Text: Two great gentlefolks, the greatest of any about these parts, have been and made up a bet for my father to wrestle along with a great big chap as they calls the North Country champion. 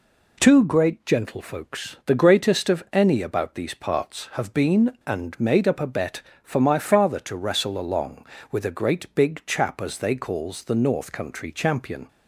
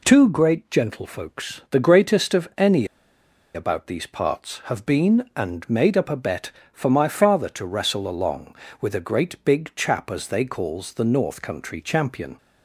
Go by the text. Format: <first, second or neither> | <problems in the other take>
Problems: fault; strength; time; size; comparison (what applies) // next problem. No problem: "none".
first | pauses between "any" and "about"; noticeable; at 2.8 s; 0.69 s long